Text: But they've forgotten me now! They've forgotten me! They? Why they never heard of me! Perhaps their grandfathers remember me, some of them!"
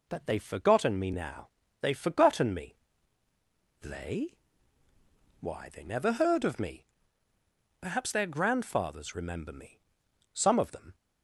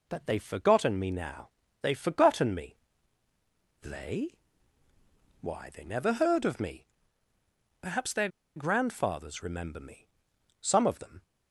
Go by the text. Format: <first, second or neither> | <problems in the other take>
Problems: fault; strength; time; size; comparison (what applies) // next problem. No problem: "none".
first | pauses between "their" and "grandfathers"; slight; at 8.2 s; 0.27 s long